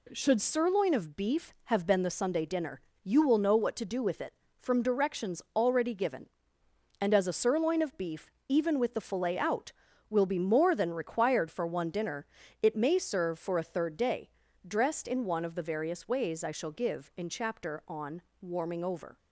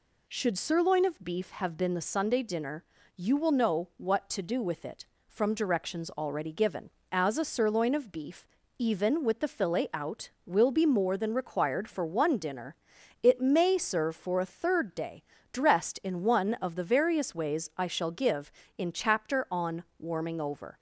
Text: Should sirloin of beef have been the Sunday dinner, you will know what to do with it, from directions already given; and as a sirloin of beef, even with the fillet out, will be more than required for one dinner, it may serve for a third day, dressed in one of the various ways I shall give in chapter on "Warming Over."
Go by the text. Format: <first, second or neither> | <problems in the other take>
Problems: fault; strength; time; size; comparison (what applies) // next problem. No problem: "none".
first | skips "and"; at 7.0 s // pauses between "on" and "Warming"; slight; at 19.8 s; 0.16 s long; slight in the first